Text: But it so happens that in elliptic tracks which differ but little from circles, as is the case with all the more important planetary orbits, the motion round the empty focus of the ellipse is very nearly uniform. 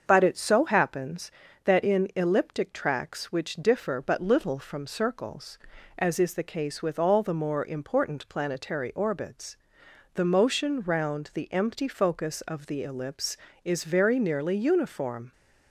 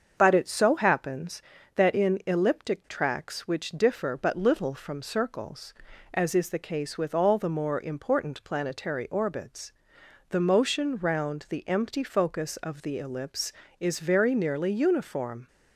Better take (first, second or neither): neither